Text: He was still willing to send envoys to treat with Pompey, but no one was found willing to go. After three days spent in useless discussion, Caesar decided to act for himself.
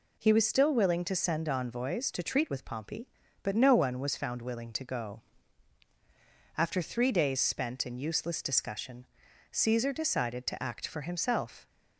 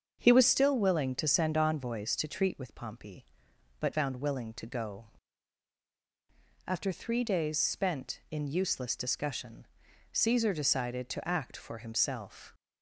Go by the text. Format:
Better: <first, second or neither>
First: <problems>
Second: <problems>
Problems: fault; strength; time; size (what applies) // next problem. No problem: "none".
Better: first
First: none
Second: starts louder than the rest; until 1.2 s; 6.5 dB // skips "no one was"; at 3.9 s